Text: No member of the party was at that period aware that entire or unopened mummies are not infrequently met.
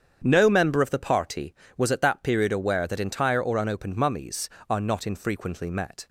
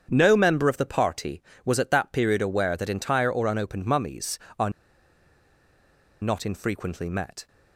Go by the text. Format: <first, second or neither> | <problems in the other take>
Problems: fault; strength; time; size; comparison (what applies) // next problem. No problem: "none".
first | starts louder than the rest; strong; until 1.1 s; 8 dB; strong in the first // pauses between "are" and "not"; strong; at 4.6 s; 1.5 s long